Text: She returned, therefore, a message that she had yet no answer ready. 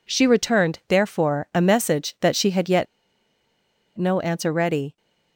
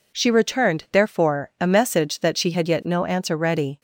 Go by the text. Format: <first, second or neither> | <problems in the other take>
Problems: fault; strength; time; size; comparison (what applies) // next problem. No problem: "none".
second | pauses between "yet" and "no"; at 2.8 s; 1.1 s long